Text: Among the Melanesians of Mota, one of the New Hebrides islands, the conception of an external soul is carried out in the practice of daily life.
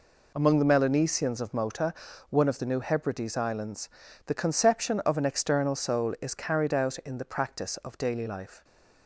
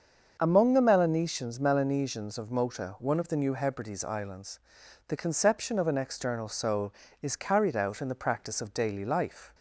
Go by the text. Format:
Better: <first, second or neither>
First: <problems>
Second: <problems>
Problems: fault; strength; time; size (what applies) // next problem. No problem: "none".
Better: first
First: none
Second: starts louder than the rest; until 1.4 s; 6.5 dB // says "Melanesians" twice; at 1.6 s